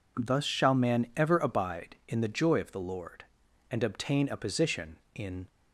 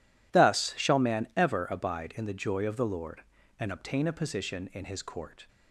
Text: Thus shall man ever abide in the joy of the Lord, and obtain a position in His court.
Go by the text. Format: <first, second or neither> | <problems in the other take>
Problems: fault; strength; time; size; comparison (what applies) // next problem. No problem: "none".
second | stops before "His court"; at 5.4 s